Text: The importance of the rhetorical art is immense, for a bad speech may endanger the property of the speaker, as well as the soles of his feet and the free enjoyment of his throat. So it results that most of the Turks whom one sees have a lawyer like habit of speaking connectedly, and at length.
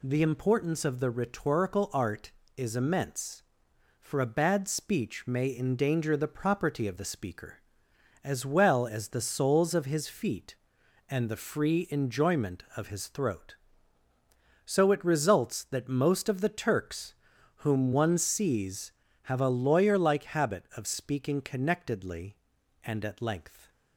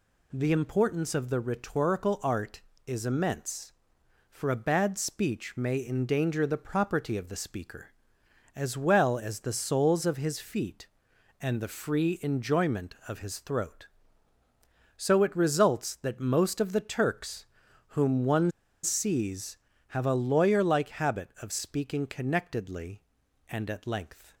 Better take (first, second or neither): first